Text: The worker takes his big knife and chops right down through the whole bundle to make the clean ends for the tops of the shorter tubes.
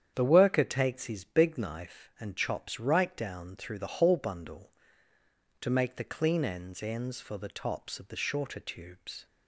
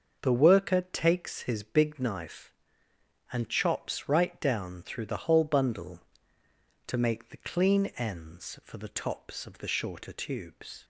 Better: second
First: starts louder than the rest; strong; until 1.1 s; 8.5 dB // says "ends" twice; at 6.8 s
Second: starts louder than the rest; until 1.2 s; 6.5 dB

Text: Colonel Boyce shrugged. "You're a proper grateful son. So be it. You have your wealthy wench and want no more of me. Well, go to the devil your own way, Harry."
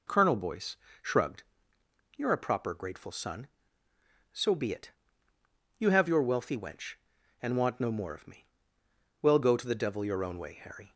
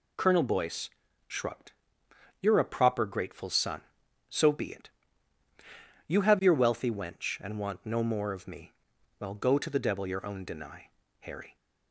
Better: first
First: pauses between "Boyce" and "shrugged"; slight; at 0.7 s; 0.24 s long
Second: pauses between "Boyce" and "shrugged"; slight; at 0.9 s; 0.36 s long // says "deny" for "way"; at 10.4 s

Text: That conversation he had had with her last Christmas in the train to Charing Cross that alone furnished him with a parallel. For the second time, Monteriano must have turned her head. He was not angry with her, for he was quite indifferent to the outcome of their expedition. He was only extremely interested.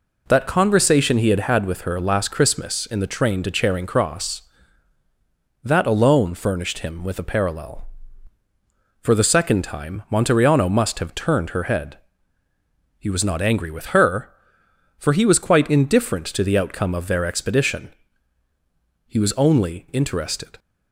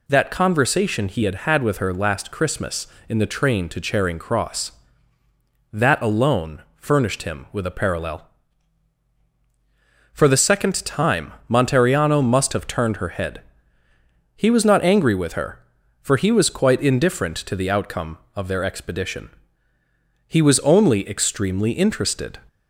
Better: second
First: skips "extremely"; at 19.8 s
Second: none

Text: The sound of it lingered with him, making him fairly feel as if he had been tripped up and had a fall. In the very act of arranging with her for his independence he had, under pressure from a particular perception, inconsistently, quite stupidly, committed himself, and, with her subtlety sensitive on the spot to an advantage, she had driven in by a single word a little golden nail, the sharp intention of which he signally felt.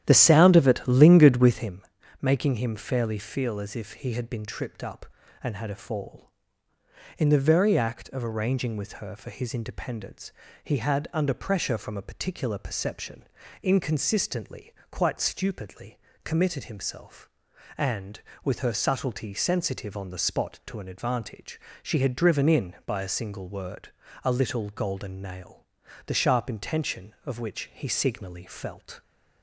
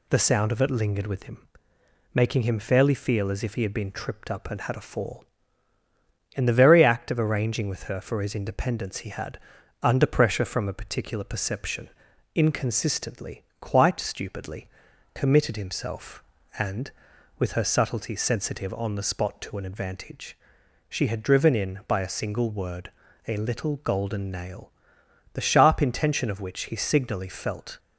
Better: second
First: starts louder than the rest; strong; until 1.8 s; 11 dB // pauses between "independence" and "he"; slight; at 10.2 s; 0.32 s long // pauses between "word" and "a"; slight; at 23.8 s; 0.34 s long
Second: pauses between "word" and "a"; slight; at 22.9 s; 0.36 s long

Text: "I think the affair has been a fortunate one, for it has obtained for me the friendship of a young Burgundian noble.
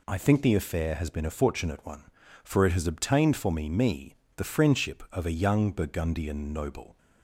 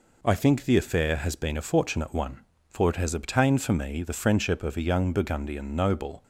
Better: second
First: says "me" twice; at 3.6 s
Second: none

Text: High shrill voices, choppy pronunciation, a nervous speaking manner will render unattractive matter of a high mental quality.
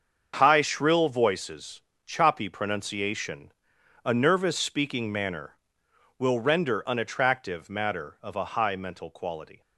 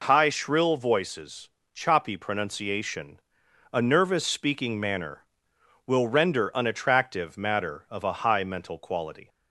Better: second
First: gets quieter; strong; throughout; 10 dB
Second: none

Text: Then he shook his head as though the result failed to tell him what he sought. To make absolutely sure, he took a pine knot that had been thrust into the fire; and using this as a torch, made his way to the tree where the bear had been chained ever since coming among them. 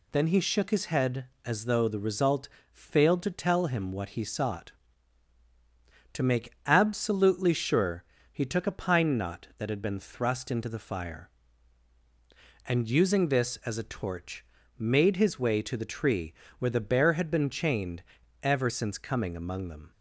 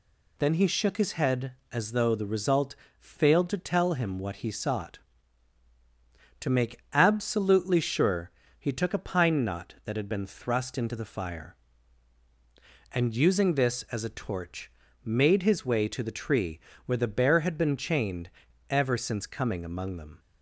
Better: neither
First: pauses between "result" and "failed"; slight; at 2.4 s; 0.26 s long // pauses between "tree" and "where"; slight; at 16.3 s; 0.25 s long // pauses between "chained" and "ever"; at 18.0 s; 0.40 s long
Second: pauses between "result" and "failed"; slight; at 2.7 s; 0.26 s long // pauses between "tree" and "where"; slight; at 16.5 s; 0.26 s long // pauses between "chained" and "ever"; at 18.2 s; 0.40 s long

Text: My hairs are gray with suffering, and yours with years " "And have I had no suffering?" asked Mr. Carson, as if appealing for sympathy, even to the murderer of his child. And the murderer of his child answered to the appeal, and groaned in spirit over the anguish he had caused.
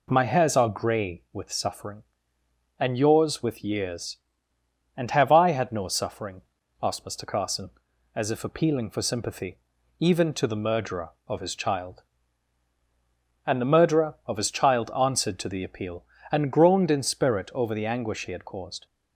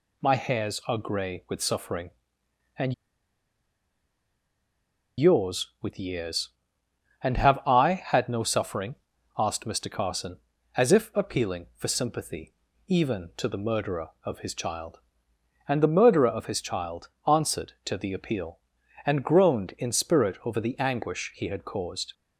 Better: first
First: none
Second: pauses between "and" and "yours"; strong; at 2.9 s; 2.2 s long // pauses between "child" and "answered"; slight; at 17.0 s; 0.18 s long

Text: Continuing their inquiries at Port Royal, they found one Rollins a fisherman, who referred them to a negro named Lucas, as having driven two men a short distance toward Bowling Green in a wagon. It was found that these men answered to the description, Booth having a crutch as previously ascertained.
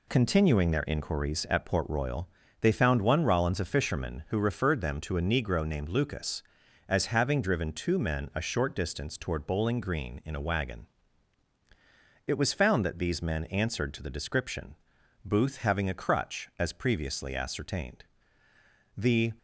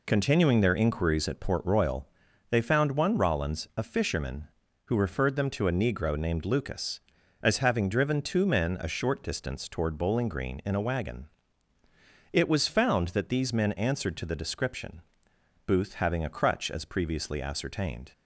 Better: second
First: goes on to say "The"; slight; from 18.9 s on; 0.36 s long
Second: none

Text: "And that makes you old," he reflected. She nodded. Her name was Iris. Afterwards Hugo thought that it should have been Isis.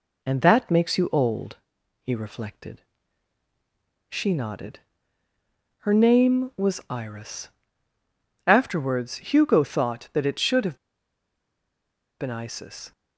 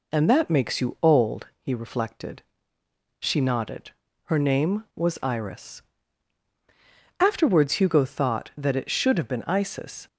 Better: second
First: pauses between "have" and "been"; strong; at 10.7 s; 1.4 s long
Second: none

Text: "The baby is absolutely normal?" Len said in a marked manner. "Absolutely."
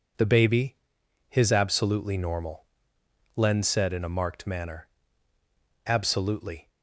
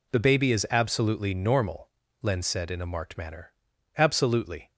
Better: second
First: says "his" for "is"; at 1.2 s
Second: none

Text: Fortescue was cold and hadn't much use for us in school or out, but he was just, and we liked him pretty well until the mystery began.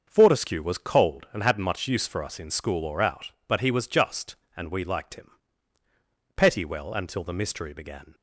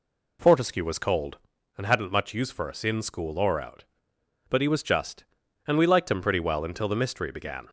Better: second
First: starts louder than the rest; until 1.0 s; 6.5 dB // says "petty" for "pretty"; at 6.3 s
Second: none

